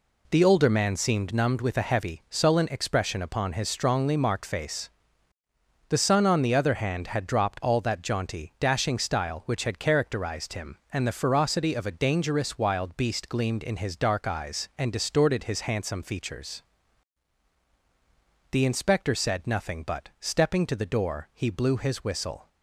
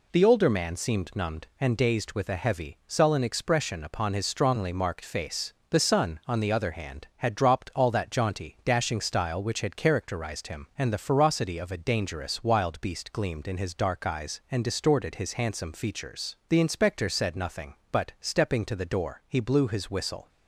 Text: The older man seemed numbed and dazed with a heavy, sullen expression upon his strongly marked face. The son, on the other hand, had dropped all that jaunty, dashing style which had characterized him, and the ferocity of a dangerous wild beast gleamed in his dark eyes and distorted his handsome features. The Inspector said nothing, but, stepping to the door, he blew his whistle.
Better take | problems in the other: second | skips "and dazed"; at 1.6 s

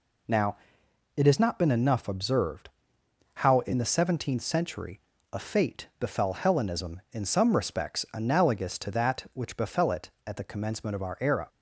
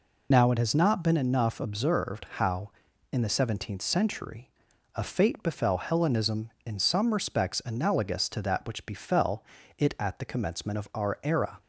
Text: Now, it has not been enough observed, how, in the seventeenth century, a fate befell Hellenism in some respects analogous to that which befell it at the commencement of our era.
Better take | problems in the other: first | loses the start of "Now"; at 0.3 s; 30 ms // pauses between "befell" and "it"; slight; at 9.4 s; 0.34 s long

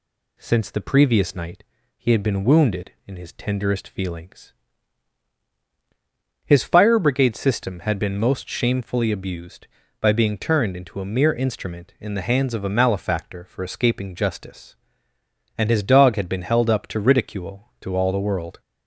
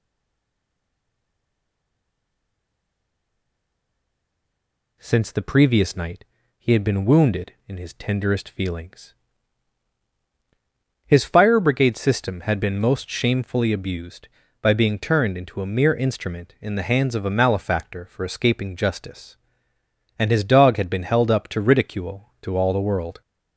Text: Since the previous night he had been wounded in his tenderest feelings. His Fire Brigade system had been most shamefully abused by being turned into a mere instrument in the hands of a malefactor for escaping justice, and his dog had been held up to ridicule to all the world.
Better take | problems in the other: first | stays silent before the first word; strong; until 4.9 s; 4.9 s long // pauses between "night" and "he"; slight; at 6.2 s; 0.32 s long; slight in the first

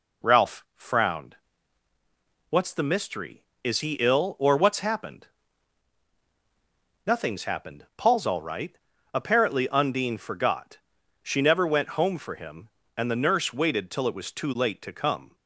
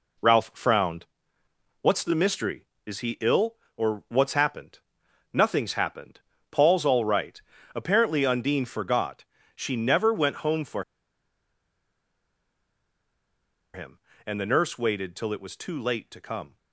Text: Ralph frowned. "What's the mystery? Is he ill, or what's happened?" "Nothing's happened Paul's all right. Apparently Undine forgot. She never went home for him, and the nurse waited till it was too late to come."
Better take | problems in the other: first | pauses between "happened" and "Paul's"; slight; at 6.2 s; 0.28 s long // pauses between "for" and "him"; strong; at 10.8 s; 2.9 s long

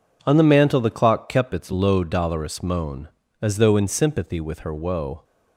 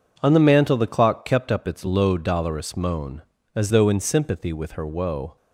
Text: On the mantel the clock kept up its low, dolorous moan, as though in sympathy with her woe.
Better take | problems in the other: second | skips "up"; at 1.5 s

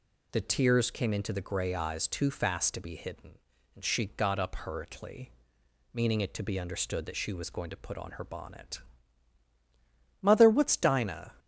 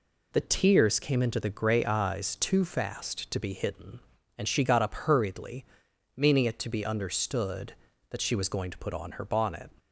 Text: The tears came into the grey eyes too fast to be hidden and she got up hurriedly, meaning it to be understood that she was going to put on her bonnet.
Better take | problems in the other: second | goes on to say "Mother what's Dinah"; noticeable; from 10.2 s on; 1.1 s long

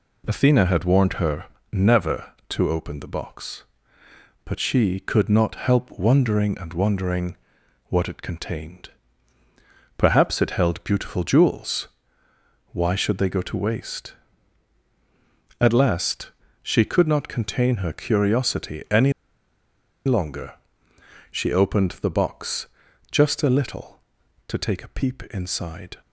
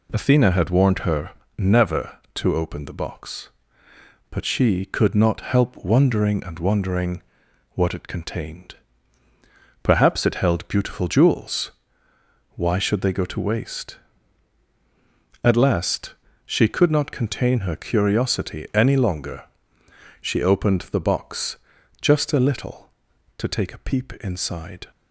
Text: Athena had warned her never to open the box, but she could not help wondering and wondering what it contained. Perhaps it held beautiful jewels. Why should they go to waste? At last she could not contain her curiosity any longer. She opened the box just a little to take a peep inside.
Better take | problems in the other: second | pauses between "her" and "never"; slight; at 1.4 s; 0.26 s long; slight in the second // pauses between "wondering" and "what"; noticeable; at 7.3 s; 0.52 s long; noticeable in the second // pauses between "last" and "she"; slight; at 16.3 s; 0.32 s long; slight in the second // pauses between "any" and "longer"; noticeable; at 19.1 s; 0.94 s long // pauses between "box" and "just"; at 22.6 s; 0.44 s long; also in the second

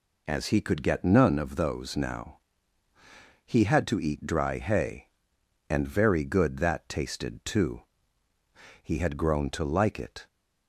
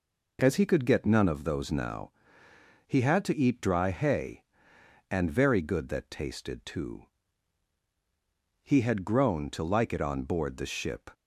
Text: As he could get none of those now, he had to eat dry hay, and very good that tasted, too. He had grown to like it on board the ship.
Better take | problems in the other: second | stops before "on board the ship"; at 10.2 s

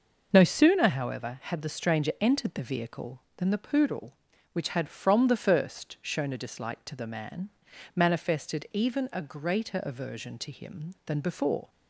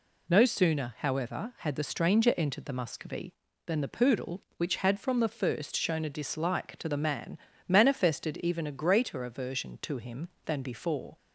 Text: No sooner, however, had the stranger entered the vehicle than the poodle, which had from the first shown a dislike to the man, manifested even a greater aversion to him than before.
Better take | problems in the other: first | says "muscovy" for "vehicle"; at 2.7 s

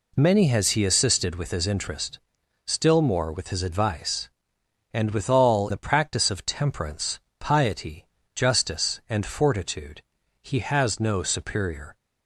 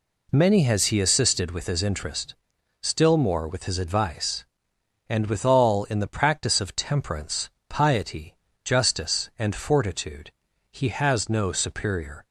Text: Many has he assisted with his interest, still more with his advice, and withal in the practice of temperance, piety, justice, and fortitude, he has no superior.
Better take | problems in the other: second | skips "in"; at 5.7 s

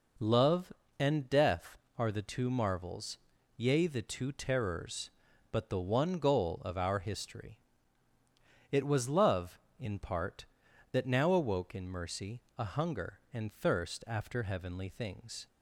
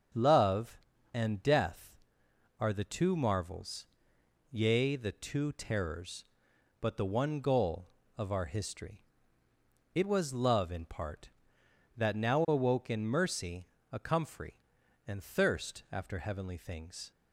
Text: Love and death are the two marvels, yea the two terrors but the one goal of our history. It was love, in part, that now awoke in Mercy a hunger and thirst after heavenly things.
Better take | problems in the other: first | starts louder than the rest; until 1.5 s; 6.5 dB // pauses between "Mercy" and "a"; slight; at 13.6 s; 0.24 s long; slight in the first // says "comfrey" for "hunger"; at 13.9 s

